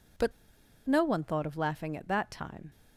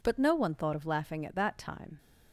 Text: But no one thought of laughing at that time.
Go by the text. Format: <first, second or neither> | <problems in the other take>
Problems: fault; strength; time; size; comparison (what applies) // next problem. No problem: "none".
second | pauses between "But" and "no"; noticeable; at 0.3 s; 0.54 s long